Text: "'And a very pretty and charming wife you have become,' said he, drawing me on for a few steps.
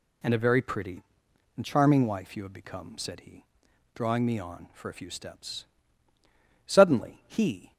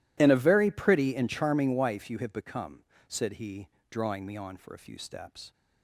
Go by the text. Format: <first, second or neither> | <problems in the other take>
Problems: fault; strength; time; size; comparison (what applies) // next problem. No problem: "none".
second | goes on to say "Suddenly he"; noticeable; from 6.6 s on; 1.0 s long